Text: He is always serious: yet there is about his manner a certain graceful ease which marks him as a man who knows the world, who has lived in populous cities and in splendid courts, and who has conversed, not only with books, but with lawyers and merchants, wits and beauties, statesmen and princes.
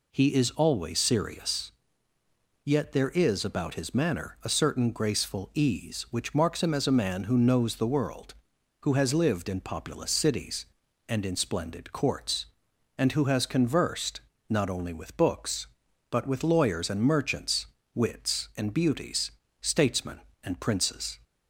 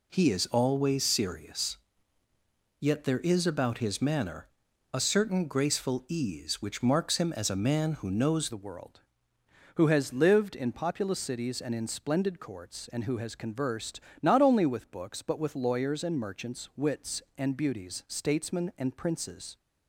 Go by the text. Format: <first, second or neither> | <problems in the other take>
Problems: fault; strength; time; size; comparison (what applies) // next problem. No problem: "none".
first | pauses between "manner" and "a"; at 4.4 s; 0.44 s long // changes voice at "the"; from 8.4 s on; 11.1 s long